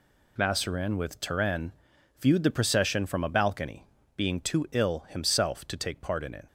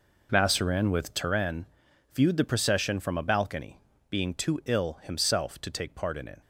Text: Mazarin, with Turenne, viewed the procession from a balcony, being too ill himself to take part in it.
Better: first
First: none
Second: starts louder than the rest; noticeable; until 1.4 s; 4.5 dB

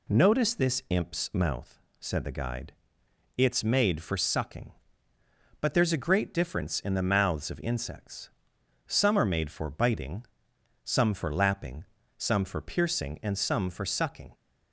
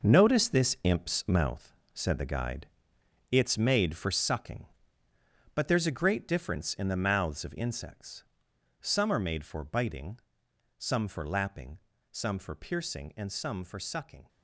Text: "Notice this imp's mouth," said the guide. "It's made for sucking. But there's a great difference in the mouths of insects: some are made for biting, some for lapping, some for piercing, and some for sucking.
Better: first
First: none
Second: gets quieter; strong; throughout; 10.5 dB

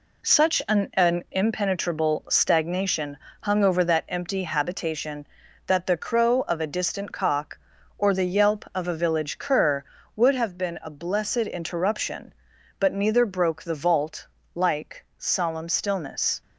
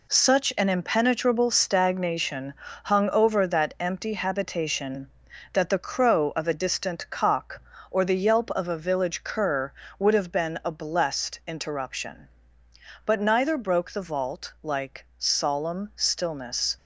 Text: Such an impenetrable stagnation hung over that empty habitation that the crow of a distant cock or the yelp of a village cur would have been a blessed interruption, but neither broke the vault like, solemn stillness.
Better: second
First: says "an" twice; at 0.9 s // pauses between "stagnation" and "hung"; slight; at 3.1 s; 0.24 s long // pauses between "vault" and "like"; slight; at 14.2 s; 0.26 s long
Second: pauses between "stagnation" and "hung"; slight; at 2.5 s; 0.30 s long

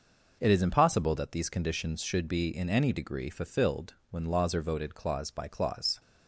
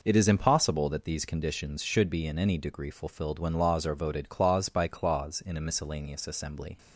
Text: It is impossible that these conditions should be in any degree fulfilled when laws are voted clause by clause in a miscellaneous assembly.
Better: second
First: pauses between "fulfilled" and "when"; slight; at 3.9 s; 0.16 s long // stops before "in a miscellaneous assembly"; at 5.9 s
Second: none

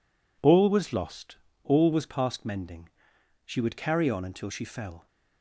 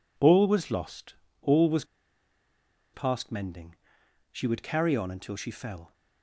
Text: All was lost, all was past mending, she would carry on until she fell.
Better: first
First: none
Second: pauses between "was" and "past"; at 1.8 s; 1.0 s long

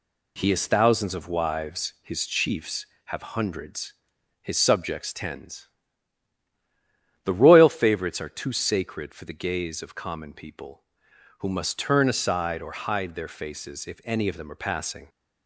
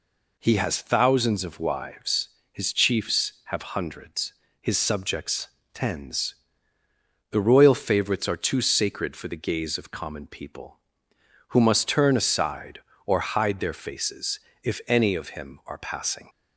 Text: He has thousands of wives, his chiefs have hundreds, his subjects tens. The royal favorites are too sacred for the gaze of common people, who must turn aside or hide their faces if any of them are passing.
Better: first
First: none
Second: pauses between "subjects" and "tens"; slight; at 5.4 s; 0.26 s long // pauses between "faces" and "if"; slight; at 14.3 s; 0.24 s long // says "him" for "them"; at 15.2 s

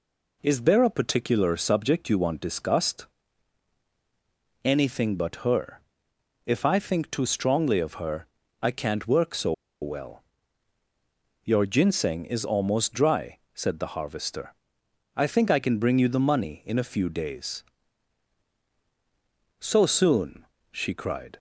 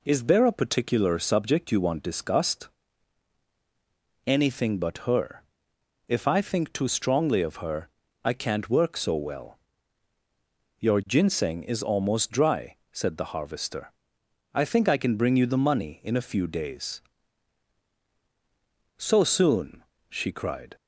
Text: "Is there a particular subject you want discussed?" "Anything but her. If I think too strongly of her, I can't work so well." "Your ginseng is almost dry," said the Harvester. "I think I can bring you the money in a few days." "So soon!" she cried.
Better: second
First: pauses between "so" and "well"; slight; at 9.5 s; 0.29 s long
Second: none

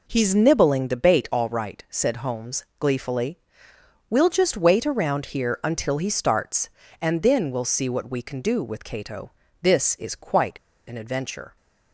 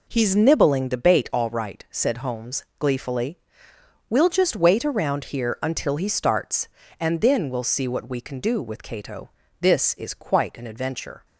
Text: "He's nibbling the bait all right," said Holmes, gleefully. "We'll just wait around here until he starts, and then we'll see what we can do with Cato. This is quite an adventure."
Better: second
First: pauses between "quite" and "an"; slight; at 10.5 s; 0.31 s long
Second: none

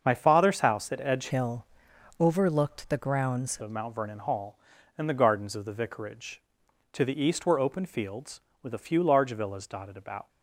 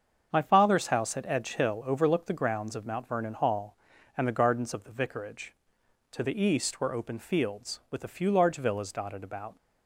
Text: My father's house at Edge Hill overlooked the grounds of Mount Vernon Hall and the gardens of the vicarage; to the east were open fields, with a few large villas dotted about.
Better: second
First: starts louder than the rest; until 1.0 s; 6.5 dB // changes voice from "Hill" to "grounds"; from 1.2 to 3.5 s; 2.3 s long // pauses between "Hill" and "overlooked"; noticeable; at 1.6 s; 0.54 s long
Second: starts louder than the rest; until 1.3 s; 7 dB

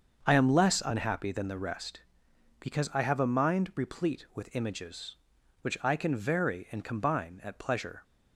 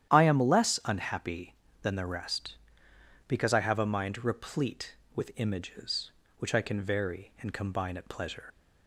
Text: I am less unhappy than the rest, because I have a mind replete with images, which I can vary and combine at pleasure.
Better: first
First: starts louder than the rest; until 1.2 s; 6.5 dB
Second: starts louder than the rest; strong; until 1.1 s; 10.5 dB // leaves "pleasure" unfinished; at 8.5 s; 75 ms

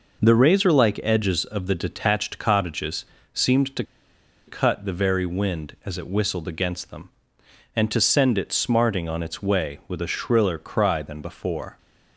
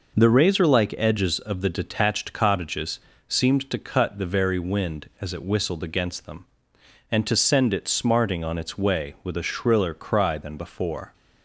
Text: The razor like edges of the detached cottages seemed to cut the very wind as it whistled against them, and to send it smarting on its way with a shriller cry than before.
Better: second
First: pauses between "cottages" and "seemed"; slight; at 3.0 s; 0.26 s long // pauses between "to" and "cut"; noticeable; at 3.8 s; 0.62 s long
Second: pauses between "cottages" and "seemed"; slight; at 3.0 s; 0.26 s long

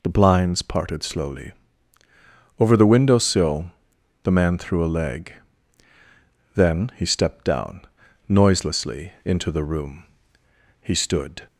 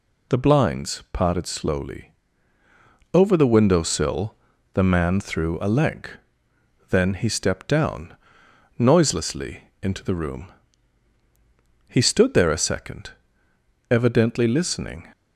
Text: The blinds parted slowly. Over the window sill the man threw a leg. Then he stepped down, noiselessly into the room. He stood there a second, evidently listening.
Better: second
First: pauses between "sill" and "the"; noticeable; at 3.7 s; 0.52 s long // stops before "there a second evidently listening"; at 11.4 s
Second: pauses between "sill" and "the"; at 4.3 s; 0.38 s long

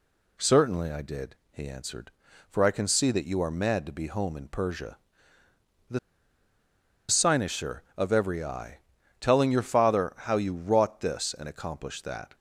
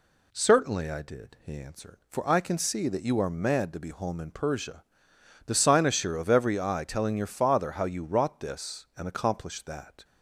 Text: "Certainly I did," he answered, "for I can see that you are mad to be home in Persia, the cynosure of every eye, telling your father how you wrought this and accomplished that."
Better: second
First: pauses between "the" and "cynosure"; at 5.9 s; 1.0 s long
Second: none

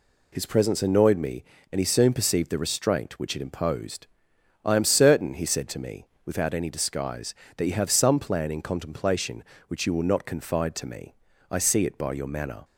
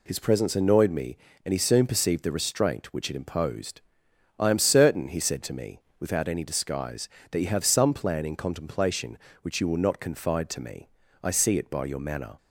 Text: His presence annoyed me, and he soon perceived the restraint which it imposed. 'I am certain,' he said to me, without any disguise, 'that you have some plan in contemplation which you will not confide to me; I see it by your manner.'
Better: neither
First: none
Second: none

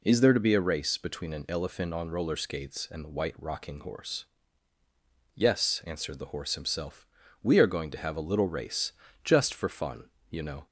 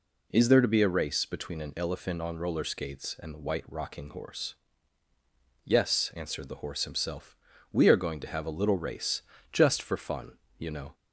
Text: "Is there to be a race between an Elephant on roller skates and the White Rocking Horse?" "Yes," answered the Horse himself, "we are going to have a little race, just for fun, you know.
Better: neither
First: none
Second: none

